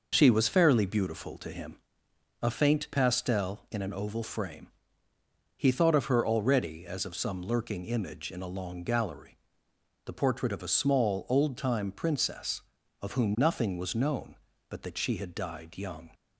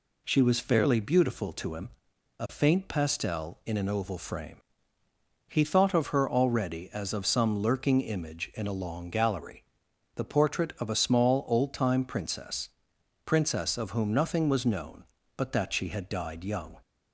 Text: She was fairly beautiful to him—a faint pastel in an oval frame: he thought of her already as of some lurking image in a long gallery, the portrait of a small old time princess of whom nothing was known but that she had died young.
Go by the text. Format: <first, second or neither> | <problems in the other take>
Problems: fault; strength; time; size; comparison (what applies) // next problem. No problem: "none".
first | says "princess" twice; at 13.2 s